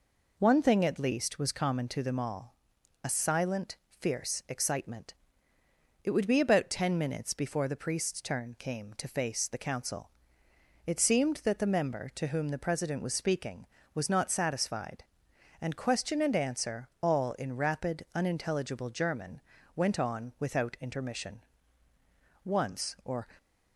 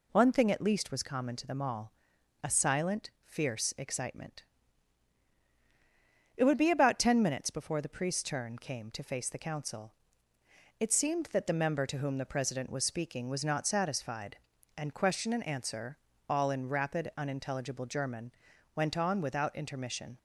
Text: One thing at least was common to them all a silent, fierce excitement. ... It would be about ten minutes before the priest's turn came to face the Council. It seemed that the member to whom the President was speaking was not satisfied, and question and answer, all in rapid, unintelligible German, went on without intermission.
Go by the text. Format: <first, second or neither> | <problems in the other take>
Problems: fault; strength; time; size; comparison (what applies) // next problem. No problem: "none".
second | pauses between "all" and "a"; noticeable; at 2.5 s; 0.50 s long; noticeable in the second // goes on to say "Once or"; noticeable; from 22.4 s on; 0.82 s long